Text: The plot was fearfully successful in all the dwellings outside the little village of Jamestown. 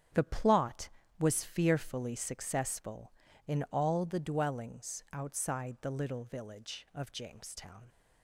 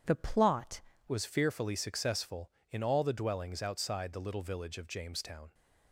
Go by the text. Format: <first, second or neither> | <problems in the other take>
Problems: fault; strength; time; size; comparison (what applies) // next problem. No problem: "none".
first | starts louder than the rest; strong; until 1.3 s; 8 dB; strong in the first // changes voice at "was"; from 1.0 s on; 4.5 s long